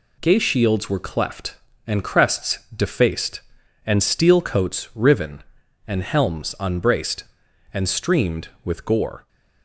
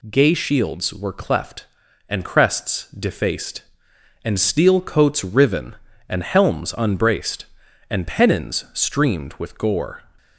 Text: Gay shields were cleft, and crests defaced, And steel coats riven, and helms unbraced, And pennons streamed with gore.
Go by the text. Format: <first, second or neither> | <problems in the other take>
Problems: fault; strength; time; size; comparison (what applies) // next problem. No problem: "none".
second | pauses between "crests" and "defaced"; slight; at 2.5 s; 0.18 s long // skips "pennons"; at 7.8 s